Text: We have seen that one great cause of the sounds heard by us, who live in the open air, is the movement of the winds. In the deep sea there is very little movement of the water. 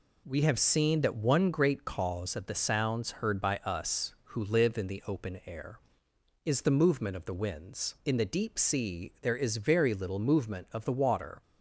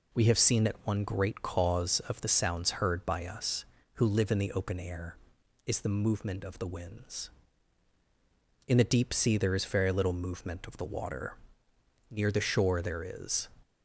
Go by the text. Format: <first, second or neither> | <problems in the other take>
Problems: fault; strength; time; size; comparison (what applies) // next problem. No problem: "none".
first | goes on to say "Near the shore there is"; from 12.0 s on; 1.3 s long